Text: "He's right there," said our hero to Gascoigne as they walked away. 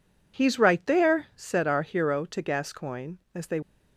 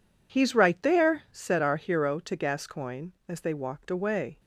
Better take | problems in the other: second | stops before "walked away"; at 3.6 s

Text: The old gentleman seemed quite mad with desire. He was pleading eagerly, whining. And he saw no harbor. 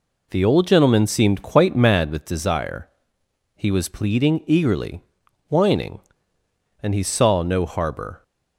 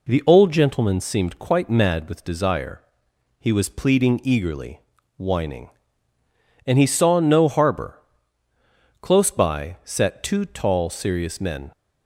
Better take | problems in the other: first | goes on to say "Close by sat two tall serious men"; strong; from 9.0 s on; 2.7 s long

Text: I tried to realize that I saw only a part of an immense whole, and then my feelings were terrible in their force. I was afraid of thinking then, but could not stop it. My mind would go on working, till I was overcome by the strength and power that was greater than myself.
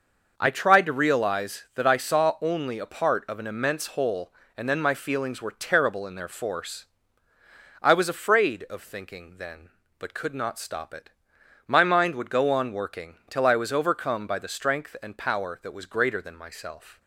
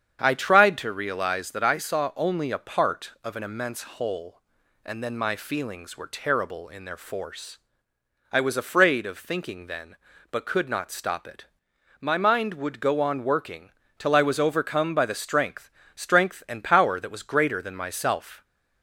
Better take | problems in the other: first | starts louder than the rest; strong; until 1.2 s; 8 dB // says "strength" twice; at 15.9 s

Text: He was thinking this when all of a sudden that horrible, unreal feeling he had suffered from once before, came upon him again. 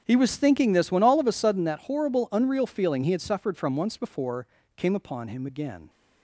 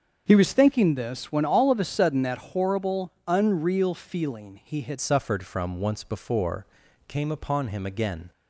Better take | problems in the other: first | starts louder than the rest; until 1.2 s; 6.5 dB; strong in the first // changes voice at "suffered"; from 4.9 s on; 3.4 s long

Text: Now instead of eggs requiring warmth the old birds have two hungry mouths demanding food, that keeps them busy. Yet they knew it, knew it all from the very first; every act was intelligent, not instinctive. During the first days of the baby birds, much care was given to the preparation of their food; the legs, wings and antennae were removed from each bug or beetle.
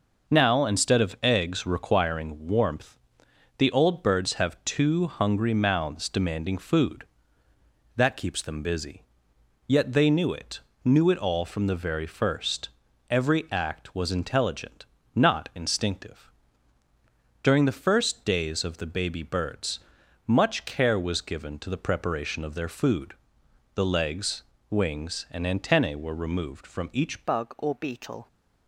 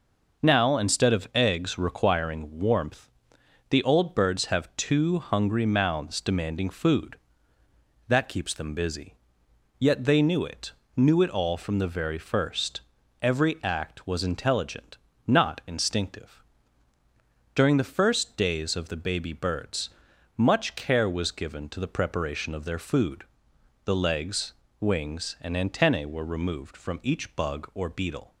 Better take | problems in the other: second | pauses between "warmth" and "the"; noticeable; at 2.9 s; 0.62 s long; noticeable in the second // changes voice at "bug"; from 27.2 s on; 1.0 s long

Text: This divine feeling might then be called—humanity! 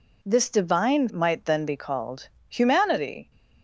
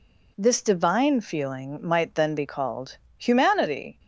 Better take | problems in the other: second | skips "feeling"; at 1.0 s

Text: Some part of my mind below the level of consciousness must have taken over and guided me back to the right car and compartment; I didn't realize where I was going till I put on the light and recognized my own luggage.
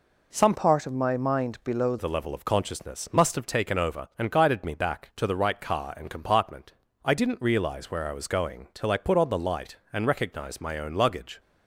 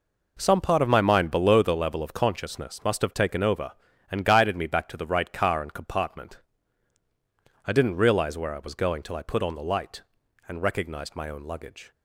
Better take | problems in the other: second | changes voice from "part" to "below"; from 0.5 to 1.9 s; 1.4 s long

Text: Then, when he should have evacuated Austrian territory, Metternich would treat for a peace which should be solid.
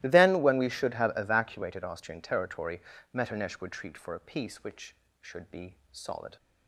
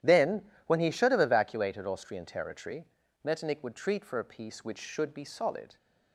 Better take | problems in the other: second | starts louder than the rest; strong; until 1.0 s; 16.5 dB; strong in the second // says "we" for "he"; at 0.5 s // pauses between "be" and "solid"; slight; at 5.7 s; 0.16 s long

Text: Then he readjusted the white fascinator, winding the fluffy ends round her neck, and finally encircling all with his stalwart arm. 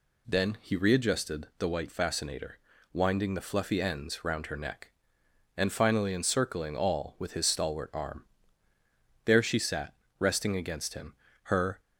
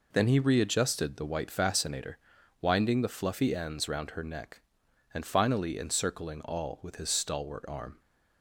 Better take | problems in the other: second | goes on to say "There she sat resting against him her"; strong; from 9.2 s on; 2.5 s long

